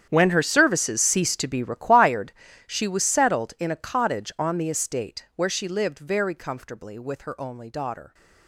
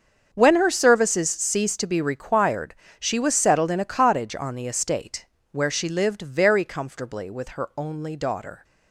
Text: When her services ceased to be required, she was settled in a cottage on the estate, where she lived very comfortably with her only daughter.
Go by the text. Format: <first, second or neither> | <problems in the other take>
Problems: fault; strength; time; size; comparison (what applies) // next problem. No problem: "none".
second | gets quieter; strong; throughout; 18 dB // starts louder than the rest; strong; until 1.1 s; 9 dB; also in the second